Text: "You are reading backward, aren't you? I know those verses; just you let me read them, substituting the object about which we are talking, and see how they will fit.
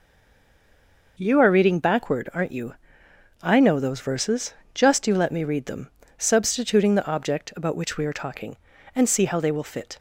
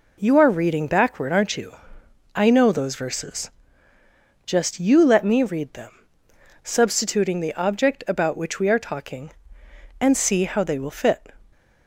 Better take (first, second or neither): second